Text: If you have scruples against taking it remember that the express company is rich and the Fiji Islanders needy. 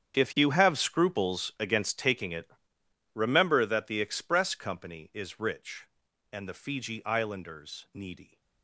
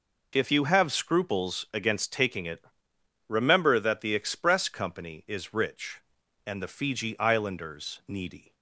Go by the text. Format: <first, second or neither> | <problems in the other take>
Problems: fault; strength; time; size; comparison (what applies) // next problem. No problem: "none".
second | gets quieter; strong; throughout; 16.5 dB // pauses between "it" and "remember"; noticeable; at 2.5 s; 0.64 s long; noticeable in the second